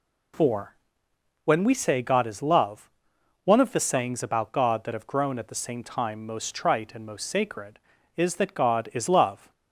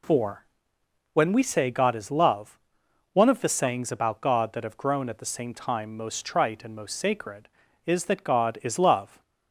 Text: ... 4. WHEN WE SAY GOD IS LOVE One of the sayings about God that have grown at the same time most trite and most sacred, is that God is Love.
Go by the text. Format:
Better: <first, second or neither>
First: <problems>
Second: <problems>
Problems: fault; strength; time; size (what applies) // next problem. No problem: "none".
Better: neither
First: pauses between "LOVE" and "One"; noticeable; at 2.9 s; 0.54 s long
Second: pauses between "LOVE" and "One"; noticeable; at 2.5 s; 0.54 s long